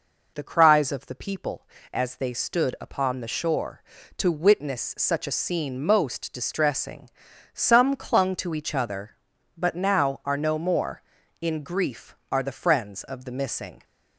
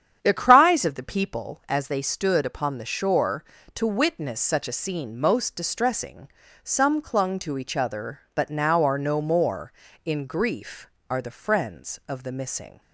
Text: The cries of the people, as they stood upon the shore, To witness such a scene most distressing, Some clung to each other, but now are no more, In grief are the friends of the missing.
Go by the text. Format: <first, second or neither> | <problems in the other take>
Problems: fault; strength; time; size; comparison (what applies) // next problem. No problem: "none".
first | starts louder than the rest; strong; until 1.5 s; 9 dB